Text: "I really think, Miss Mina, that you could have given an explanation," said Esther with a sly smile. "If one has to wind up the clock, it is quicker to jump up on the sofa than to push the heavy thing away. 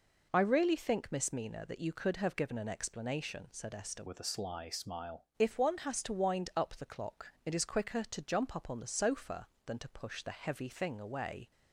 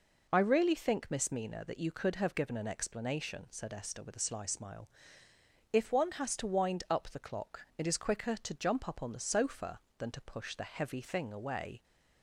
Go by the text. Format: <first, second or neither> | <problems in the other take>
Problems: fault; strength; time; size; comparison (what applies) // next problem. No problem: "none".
second | changes voice from "with" to "smile"; from 4.0 to 5.2 s; 1.2 s long